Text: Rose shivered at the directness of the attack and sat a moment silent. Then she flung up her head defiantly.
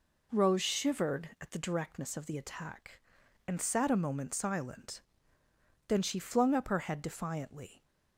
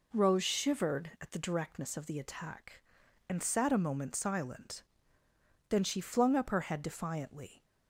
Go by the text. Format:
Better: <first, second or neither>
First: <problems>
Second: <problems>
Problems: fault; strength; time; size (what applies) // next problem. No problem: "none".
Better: neither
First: none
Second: none